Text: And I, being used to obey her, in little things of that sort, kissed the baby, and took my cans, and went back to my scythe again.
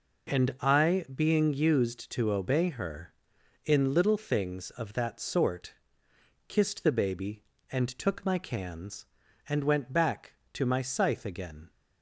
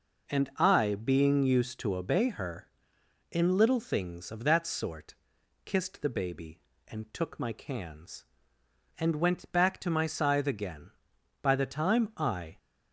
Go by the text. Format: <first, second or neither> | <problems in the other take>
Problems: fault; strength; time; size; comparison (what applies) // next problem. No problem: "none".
first | goes on to say "By the time I"; noticeable; from 11.4 s on; 1.1 s long